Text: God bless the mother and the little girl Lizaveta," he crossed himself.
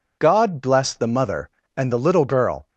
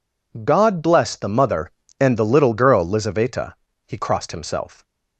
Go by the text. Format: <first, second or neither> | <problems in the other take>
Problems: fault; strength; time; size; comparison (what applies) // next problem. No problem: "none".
second | stops before "Lizaveta he crossed himself"; at 2.6 s